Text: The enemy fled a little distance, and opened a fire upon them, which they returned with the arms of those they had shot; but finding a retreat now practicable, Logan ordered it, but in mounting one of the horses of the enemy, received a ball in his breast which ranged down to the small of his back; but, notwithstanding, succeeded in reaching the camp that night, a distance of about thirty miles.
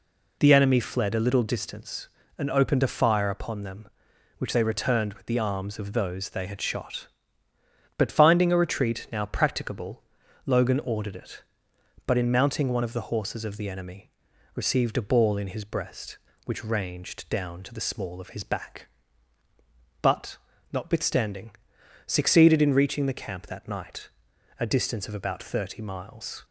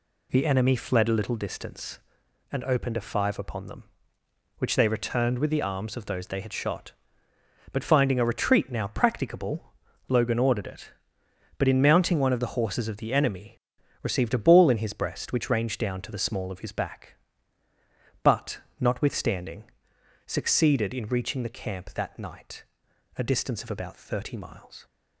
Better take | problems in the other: first | says "five" for "fire"; at 3.0 s

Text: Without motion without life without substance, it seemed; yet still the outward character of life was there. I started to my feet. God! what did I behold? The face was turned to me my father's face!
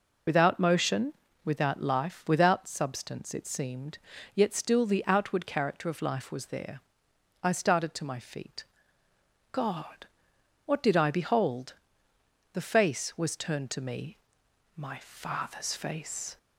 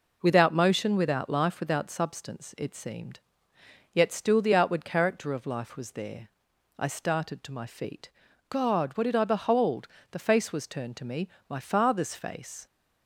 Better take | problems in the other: second | loses the start of "Without"; at 0.2 s; 45 ms // pauses between "motion" and "without"; slight; at 1.1 s; 0.30 s long // pauses between "me" and "my"; noticeable; at 14.1 s; 0.58 s long; slight in the second

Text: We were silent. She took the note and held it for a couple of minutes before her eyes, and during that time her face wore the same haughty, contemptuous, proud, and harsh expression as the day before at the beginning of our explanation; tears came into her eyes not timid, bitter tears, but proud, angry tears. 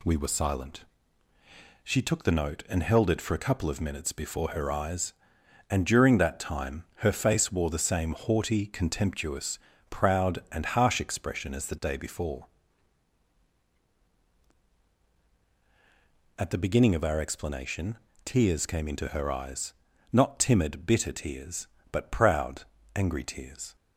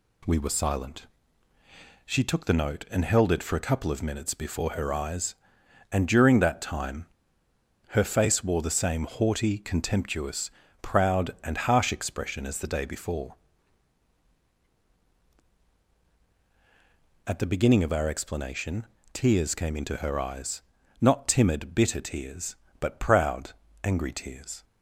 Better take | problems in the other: first | pauses between "time" and "her"; noticeable; at 7.0 s; 0.82 s long // pauses between "eyes" and "not"; at 20.6 s; 0.38 s long; also in the first

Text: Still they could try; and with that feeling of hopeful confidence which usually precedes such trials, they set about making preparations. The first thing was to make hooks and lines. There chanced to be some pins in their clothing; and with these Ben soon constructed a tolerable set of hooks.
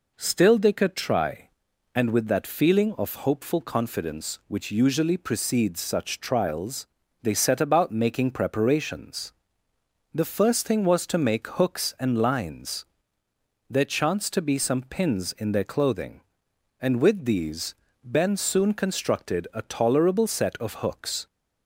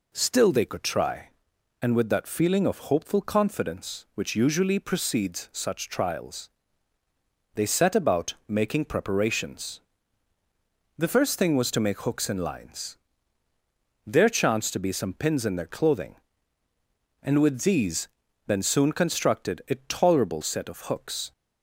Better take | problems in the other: neither | pauses between "these" and "Ben"; the same in both

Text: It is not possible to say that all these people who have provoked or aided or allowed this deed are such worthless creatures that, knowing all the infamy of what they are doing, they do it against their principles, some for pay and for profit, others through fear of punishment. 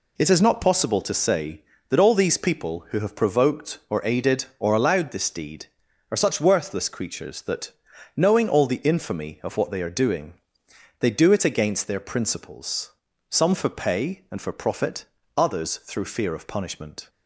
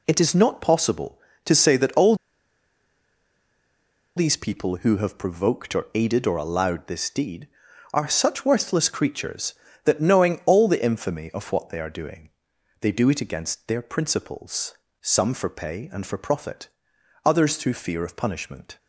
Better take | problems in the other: first | pauses between "all" and "these"; strong; at 2.1 s; 2.0 s long

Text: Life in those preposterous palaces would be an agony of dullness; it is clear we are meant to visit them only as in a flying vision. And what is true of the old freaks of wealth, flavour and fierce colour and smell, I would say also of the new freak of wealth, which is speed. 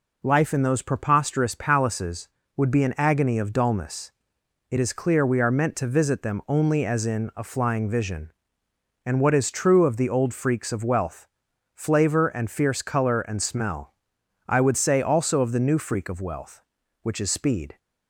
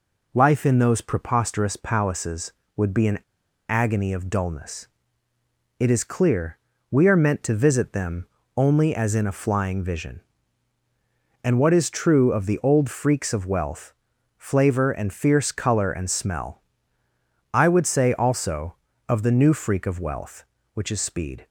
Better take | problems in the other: first | pauses between "an" and "agony"; noticeable; at 3.1 s; 0.50 s long // pauses between "clear" and "we"; slight; at 6.5 s; 0.32 s long // pauses between "them" and "only"; slight; at 8.2 s; 0.30 s long

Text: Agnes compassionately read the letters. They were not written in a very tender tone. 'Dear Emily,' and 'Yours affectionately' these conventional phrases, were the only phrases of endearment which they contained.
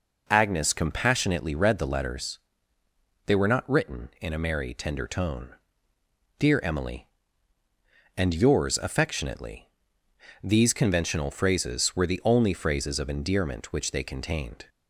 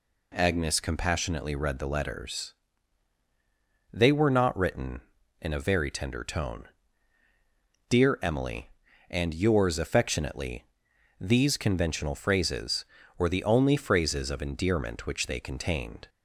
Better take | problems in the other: second | says "merry" for "very"; at 4.3 s // pauses between "affectionately" and "these"; noticeable; at 9.6 s; 0.74 s long; noticeable in the second

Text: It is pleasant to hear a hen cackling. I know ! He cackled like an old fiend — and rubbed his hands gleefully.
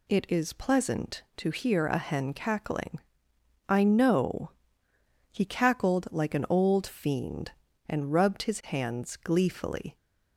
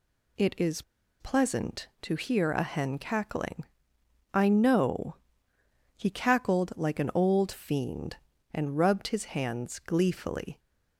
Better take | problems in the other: first | pauses between "is" and "pleasant"; at 0.8 s; 0.39 s long

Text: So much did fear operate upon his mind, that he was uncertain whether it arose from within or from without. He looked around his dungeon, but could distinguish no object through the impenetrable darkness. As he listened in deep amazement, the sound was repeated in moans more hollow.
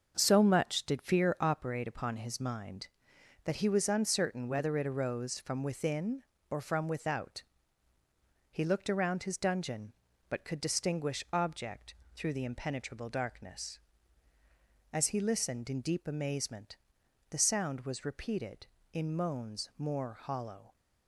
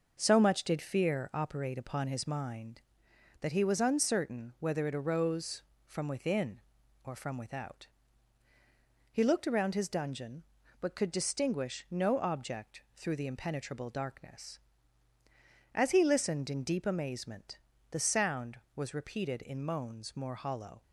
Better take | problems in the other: second | starts louder than the rest; until 1.1 s; 6.5 dB // skips "no"; at 11.2 s // pauses between "object" and "through"; slight; at 11.9 s; 0.20 s long

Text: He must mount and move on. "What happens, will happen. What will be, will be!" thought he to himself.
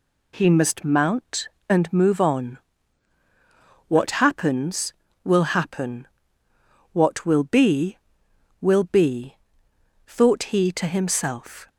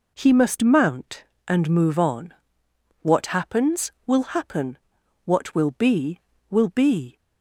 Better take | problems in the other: first | stops before "thought he to himself"; at 7.1 s

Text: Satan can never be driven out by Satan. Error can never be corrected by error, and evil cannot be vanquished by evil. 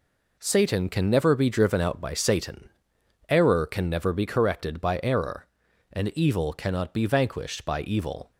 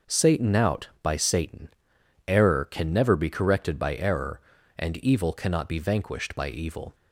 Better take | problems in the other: first | skips "can never be driven"; at 0.5 s

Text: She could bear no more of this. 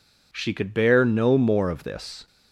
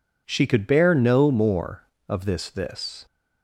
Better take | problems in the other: first | says "this" twice; at 2.4 s

